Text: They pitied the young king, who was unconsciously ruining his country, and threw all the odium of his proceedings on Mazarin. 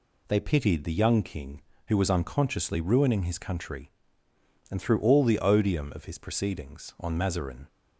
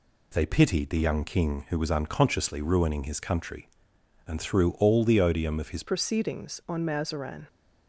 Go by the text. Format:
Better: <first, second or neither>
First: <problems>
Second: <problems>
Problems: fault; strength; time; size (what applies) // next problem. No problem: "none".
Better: first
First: none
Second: changes voice at "proceedings"; from 5.8 s on; 1.6 s long